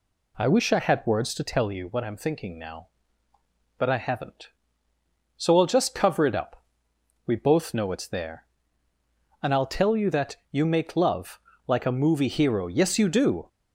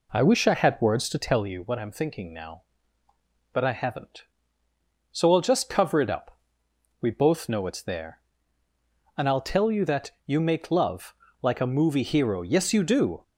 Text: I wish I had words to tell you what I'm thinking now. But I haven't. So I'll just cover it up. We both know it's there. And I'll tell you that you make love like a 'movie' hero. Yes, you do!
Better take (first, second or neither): first